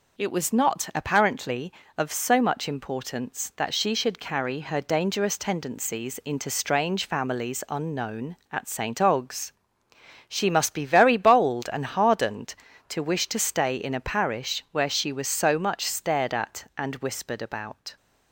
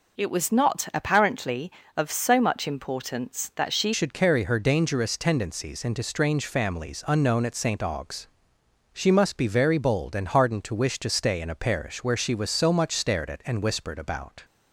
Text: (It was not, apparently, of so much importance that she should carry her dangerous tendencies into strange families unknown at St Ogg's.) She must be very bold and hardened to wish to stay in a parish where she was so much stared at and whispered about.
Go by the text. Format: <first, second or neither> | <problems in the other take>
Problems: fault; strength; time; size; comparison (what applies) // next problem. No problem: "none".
first | changes voice at "should"; from 3.9 s on; 10.5 s long